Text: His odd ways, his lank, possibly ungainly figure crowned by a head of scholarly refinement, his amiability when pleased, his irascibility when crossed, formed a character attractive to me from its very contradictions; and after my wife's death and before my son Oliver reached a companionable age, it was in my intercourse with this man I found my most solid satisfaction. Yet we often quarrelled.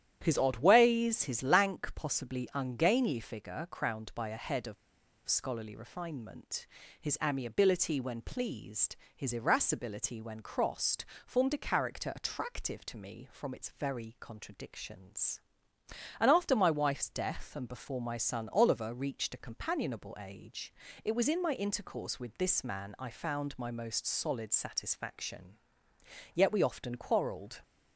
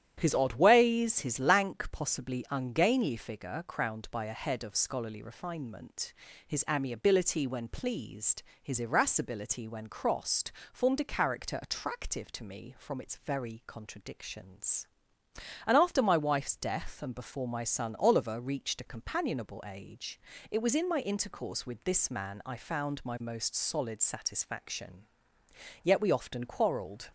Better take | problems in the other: second | starts louder than the rest; strong; until 1.2 s; 10.5 dB; strong in the second // pauses between "of" and "scholarly"; noticeable; at 4.7 s; 0.52 s long

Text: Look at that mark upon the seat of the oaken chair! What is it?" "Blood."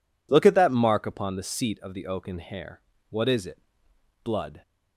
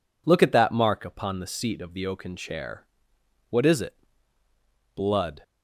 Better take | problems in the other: second | says "hair" for "chair"; at 2.3 s

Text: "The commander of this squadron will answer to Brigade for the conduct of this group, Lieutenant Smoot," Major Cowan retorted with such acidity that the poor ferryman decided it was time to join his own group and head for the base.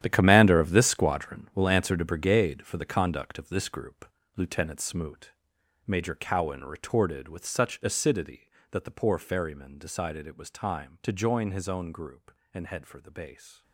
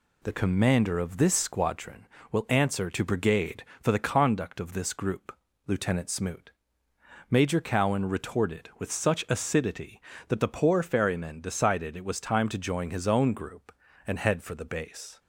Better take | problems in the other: second | gets quieter; strong; throughout; 14 dB

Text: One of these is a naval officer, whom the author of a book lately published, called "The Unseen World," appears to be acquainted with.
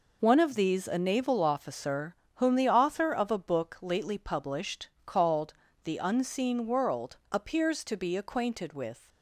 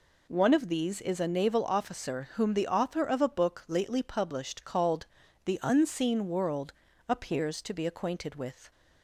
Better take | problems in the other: second | skips "is"; at 0.8 s // pauses between "called" and "The"; slight; at 5.5 s; 0.30 s long; also in the second

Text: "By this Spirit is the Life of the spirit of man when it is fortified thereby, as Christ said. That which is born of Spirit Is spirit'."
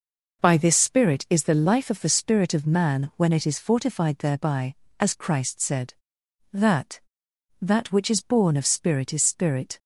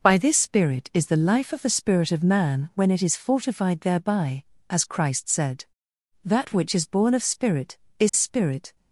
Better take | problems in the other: second | says "That" twice; at 7.5 s

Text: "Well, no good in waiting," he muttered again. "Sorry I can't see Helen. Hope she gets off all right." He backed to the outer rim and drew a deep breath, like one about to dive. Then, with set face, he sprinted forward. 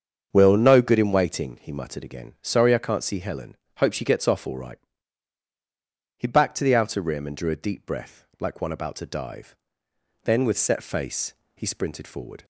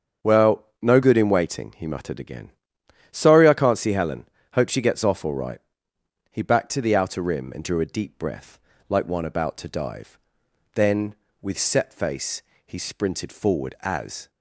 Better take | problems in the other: first | starts louder than the rest; strong; until 1.3 s; 7 dB; strong in the first // goes on to say "As"; slight; from 13.8 s on; 0.48 s long

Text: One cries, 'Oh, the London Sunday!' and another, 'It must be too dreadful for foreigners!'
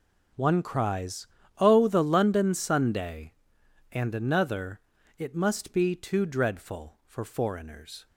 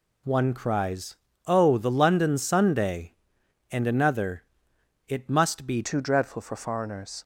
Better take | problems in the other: first | changes voice at "too"; from 5.8 s on; 1.4 s long

